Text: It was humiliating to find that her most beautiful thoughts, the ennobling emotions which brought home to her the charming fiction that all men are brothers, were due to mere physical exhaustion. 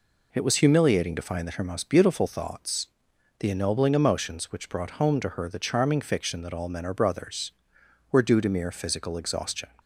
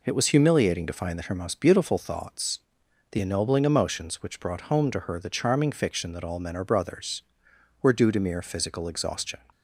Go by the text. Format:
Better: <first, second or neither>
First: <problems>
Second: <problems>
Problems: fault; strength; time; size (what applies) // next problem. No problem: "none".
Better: neither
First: none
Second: none